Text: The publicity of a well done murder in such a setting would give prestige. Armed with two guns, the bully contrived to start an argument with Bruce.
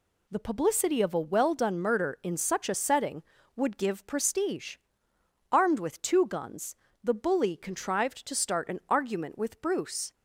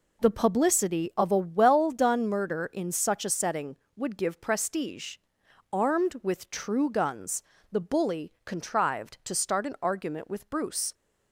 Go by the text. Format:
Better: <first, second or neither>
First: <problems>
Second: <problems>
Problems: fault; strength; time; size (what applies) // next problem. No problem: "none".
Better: first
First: none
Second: says "true" for "two"; at 6.4 s